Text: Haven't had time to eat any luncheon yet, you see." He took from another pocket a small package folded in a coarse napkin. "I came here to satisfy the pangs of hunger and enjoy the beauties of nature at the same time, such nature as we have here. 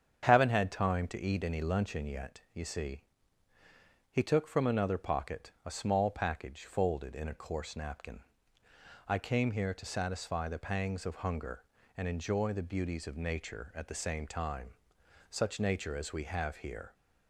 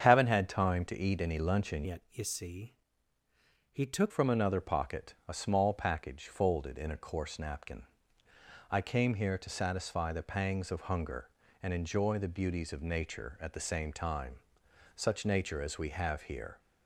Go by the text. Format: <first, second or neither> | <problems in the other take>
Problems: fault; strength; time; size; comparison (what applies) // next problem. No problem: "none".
first | starts louder than the rest; noticeable; until 1.1 s; 6 dB; also in the first // changes voice from "yet" to "took"; from 1.8 to 4.1 s; 2.3 s long